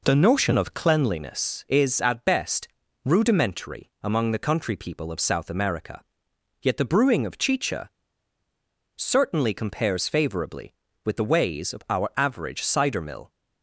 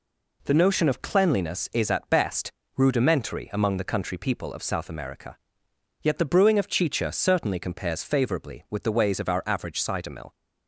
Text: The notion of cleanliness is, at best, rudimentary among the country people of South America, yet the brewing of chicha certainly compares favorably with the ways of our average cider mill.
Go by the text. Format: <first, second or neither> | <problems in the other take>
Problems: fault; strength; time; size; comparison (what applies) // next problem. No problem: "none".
second | pauses between "chicha" and "certainly"; at 7.8 s; 1.0 s long